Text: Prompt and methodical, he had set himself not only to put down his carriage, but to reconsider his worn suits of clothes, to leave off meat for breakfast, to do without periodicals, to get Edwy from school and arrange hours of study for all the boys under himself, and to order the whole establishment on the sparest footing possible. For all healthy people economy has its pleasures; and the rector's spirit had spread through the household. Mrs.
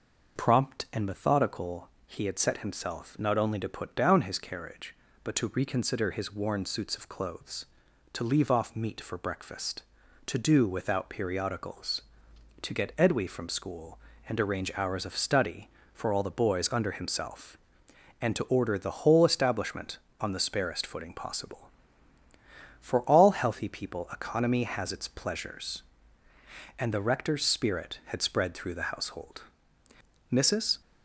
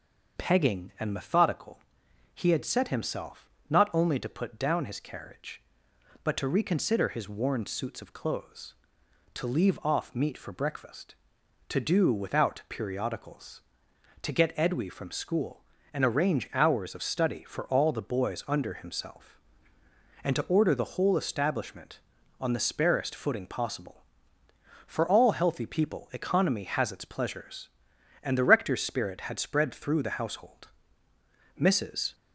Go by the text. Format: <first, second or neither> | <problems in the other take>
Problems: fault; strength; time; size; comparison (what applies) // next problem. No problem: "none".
first | starts louder than the rest; until 1.4 s; 6.5 dB // says "Pegging" for "Prompt"; at 0.3 s // pauses between "himself" and "not"; slight; at 3.4 s; 0.22 s long